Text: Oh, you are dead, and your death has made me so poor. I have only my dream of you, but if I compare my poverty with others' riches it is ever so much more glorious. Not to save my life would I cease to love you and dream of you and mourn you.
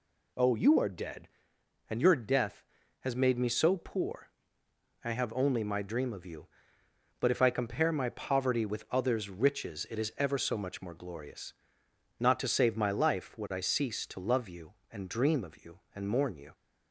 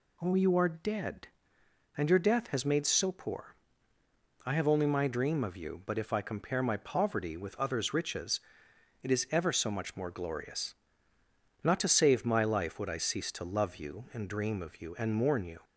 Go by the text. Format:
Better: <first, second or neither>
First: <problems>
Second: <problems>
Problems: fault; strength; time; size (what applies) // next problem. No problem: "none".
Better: first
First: none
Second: skips "me"; at 2.8 s // pauses between "riches" and "it"; noticeable; at 8.3 s; 0.62 s long